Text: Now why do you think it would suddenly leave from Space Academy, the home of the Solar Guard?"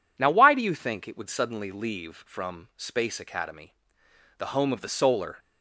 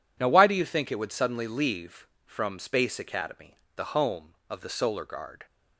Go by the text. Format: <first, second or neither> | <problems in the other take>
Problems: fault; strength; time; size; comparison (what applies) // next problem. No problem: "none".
second | stops before "Guard"; at 5.3 s